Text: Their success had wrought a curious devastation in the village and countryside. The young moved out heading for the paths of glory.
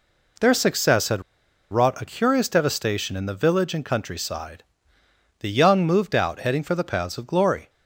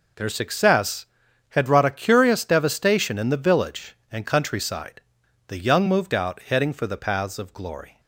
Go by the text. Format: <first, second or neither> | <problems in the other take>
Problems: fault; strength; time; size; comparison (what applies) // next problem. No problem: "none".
second | pauses between "had" and "wrought"; noticeable; at 1.2 s; 0.48 s long